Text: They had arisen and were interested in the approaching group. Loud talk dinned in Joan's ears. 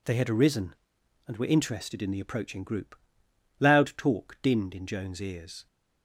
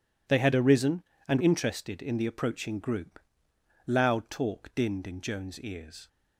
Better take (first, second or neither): first